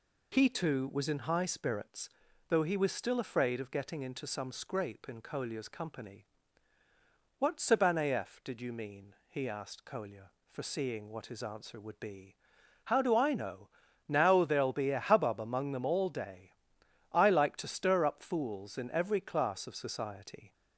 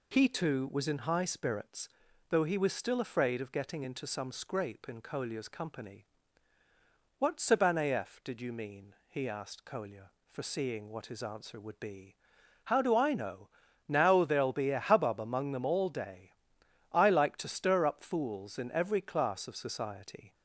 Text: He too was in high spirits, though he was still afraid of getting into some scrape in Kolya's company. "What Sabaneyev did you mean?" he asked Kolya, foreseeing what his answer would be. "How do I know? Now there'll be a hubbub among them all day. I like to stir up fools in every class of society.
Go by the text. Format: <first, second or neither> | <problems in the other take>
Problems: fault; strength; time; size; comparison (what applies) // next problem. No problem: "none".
neither | none